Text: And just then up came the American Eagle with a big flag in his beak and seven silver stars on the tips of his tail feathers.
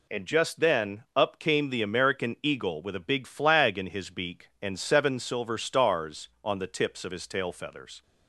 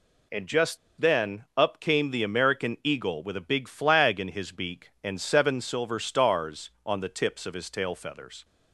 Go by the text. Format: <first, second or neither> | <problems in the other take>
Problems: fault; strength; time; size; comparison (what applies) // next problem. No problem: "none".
first | pauses between "just" and "then"; slight; at 0.7 s; 0.22 s long